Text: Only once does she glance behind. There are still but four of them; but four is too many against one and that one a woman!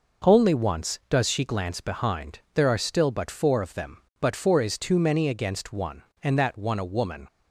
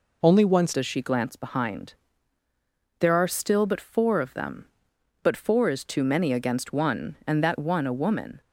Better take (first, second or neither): first